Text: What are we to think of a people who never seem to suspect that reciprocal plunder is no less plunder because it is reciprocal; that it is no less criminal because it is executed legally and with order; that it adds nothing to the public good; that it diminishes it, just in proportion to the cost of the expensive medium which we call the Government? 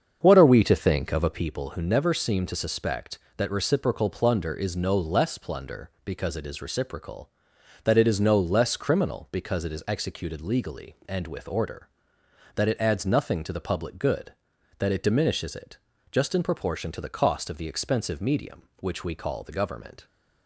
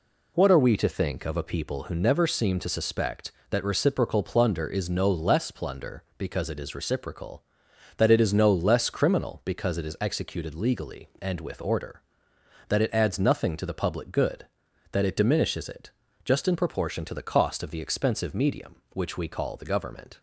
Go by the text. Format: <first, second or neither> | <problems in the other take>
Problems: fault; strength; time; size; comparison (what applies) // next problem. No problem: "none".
second | starts louder than the rest; until 1.4 s; 7 dB